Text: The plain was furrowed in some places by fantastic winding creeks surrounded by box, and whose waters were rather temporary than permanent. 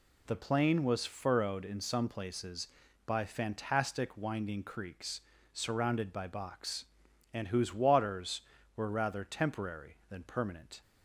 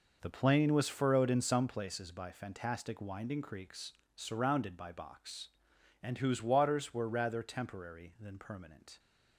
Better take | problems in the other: neither | pauses between "creeks" and "surrounded"; slight; the same in both

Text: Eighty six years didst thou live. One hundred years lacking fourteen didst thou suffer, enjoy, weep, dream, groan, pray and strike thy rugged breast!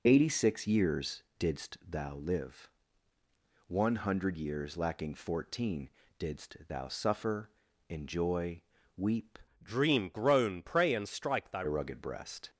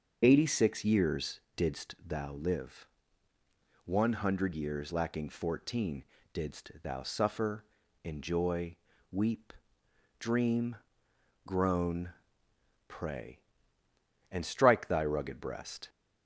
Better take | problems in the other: second | pauses between "years" and "didst"; slight; at 1.2 s; 0.16 s long; slight in the second // pauses between "fourteen" and "didst"; slight; at 5.9 s; 0.30 s long; slight in the second // changes voice from "dream" to "thy"; from 9.6 to 11.6 s; 2.0 s long

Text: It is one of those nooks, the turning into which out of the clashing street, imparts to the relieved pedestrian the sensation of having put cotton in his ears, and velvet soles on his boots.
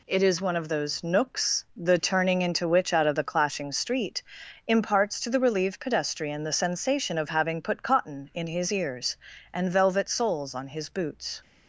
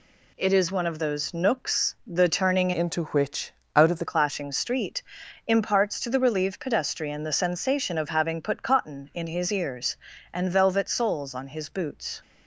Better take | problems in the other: first | changes voice from "into" to "the"; from 2.7 to 4.0 s; 1.3 s long // pauses between "which" and "out"; slight; at 3.5 s; 0.22 s long

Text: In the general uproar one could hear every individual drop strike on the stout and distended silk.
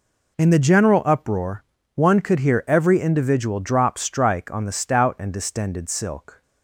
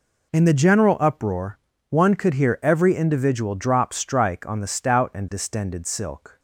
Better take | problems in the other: neither | pauses between "uproar" and "one"; slight; the same in both

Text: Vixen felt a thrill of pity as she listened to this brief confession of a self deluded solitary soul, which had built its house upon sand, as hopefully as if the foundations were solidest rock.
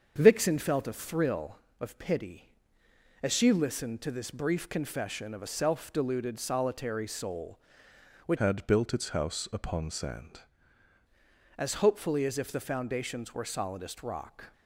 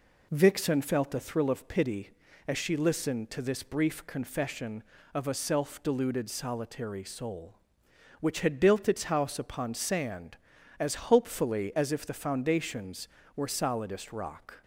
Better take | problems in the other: second | starts louder than the rest; until 1.1 s; 7 dB // changes voice from "had" to "sand"; from 8.3 to 10.4 s; 2.1 s long

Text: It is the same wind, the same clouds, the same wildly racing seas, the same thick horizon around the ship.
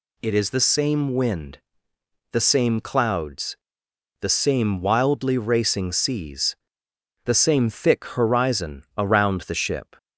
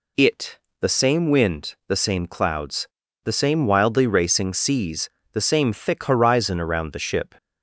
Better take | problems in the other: first | skips "is"; at 0.6 s

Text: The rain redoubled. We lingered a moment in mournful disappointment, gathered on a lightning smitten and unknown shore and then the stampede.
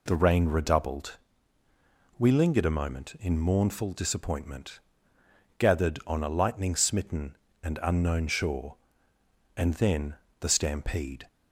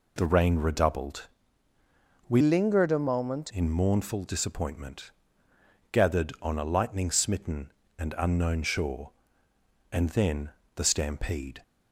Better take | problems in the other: first | changes voice from "lingered" to "moment"; from 2.3 to 3.5 s; 1.2 s long // pauses between "then" and "the"; slight; at 10.5 s; 0.26 s long; slight in the first

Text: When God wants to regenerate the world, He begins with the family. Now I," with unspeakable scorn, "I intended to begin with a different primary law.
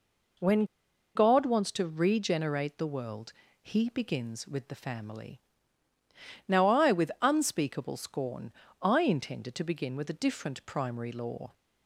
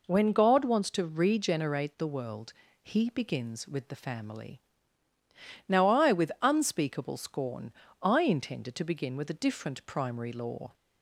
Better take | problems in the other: second | pauses between "When" and "God"; noticeable; at 0.6 s; 0.50 s long

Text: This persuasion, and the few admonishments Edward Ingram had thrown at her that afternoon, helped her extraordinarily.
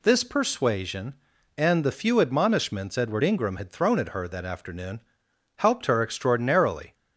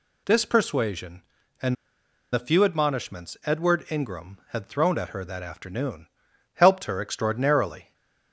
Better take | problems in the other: first | pauses between "and" and "the"; noticeable; at 1.7 s; 0.58 s long // stays silent after the last word; slight; from 7.8 s on; 0.5 s long

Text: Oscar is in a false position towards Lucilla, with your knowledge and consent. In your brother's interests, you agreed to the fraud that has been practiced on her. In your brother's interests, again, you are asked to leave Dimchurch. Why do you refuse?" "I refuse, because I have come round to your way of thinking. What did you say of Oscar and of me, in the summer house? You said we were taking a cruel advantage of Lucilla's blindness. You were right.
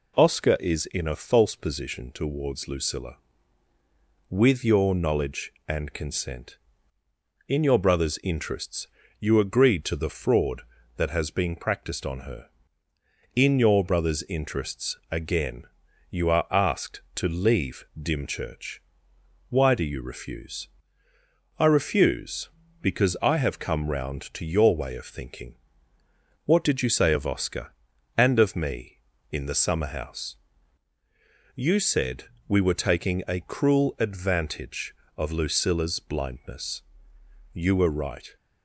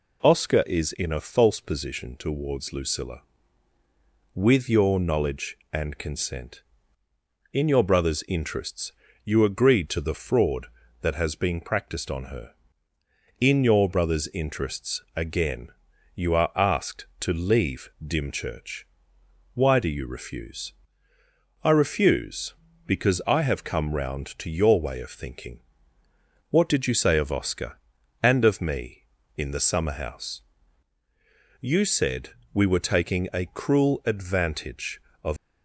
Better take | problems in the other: first | pauses between "leave" and "Dimchurch"; slight; at 17.8 s; 0.16 s long; slight in the first // pauses between "said" and "we"; slight; at 32.3 s; 0.22 s long; slight in the first // stops before "Lucilla's blindness You were right"; at 35.3 s

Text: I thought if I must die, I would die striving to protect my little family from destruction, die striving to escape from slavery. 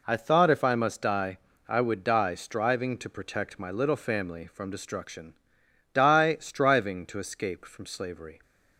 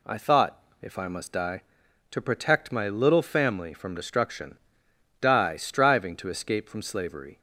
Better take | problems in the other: first | pauses between "thought" and "if"; slight; at 0.6 s; 0.20 s long // skips "I would die striving"; at 1.8 s

